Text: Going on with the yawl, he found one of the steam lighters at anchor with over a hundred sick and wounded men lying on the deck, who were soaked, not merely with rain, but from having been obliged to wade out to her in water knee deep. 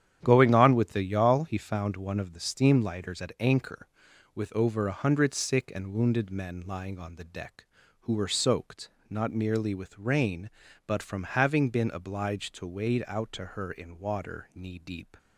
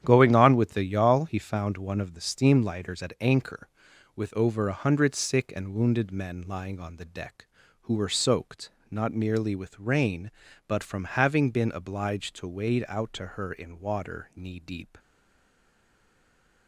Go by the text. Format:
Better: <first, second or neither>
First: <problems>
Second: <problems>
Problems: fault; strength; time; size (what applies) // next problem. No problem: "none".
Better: first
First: starts louder than the rest; strong; until 1.2 s; 10 dB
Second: starts louder than the rest; strong; until 1.0 s; 10 dB // stays silent after the last word; noticeable; from 14.9 s on; 1.7 s long